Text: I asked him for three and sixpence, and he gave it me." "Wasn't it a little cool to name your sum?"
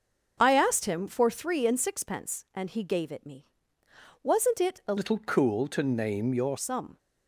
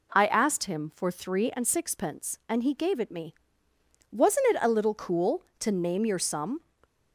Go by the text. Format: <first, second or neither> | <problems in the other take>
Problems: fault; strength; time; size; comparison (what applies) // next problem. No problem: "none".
second | changes voice from "little" to "your"; from 4.9 to 6.5 s; 1.6 s long